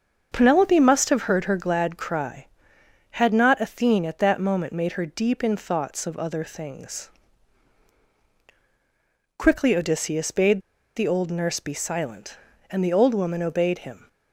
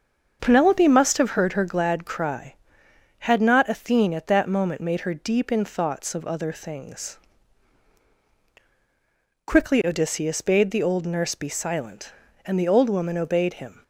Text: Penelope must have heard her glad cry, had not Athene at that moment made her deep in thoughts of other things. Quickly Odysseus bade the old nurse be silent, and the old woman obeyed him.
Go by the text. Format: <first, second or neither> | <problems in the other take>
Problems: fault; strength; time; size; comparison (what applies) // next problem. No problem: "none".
second | starts louder than the rest; until 1.3 s; 6.5 dB; also in the second // pauses between "bade" and "the"; slight; at 10.6 s; 0.35 s long